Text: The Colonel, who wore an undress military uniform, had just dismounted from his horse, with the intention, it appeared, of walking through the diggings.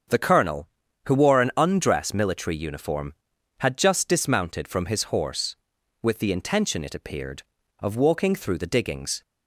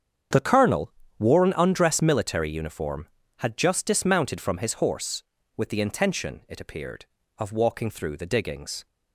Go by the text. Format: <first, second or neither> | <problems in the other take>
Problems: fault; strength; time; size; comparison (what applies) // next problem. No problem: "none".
first | starts louder than the rest; strong; until 1.6 s; 8 dB; strong in the first // skips "who"; at 1.0 s